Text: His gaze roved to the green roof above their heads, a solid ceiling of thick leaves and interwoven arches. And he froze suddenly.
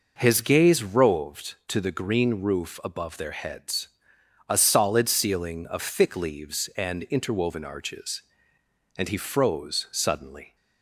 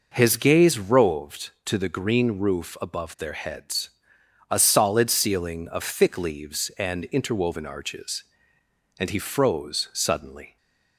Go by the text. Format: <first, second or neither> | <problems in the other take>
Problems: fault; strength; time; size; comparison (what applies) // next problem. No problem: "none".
neither | none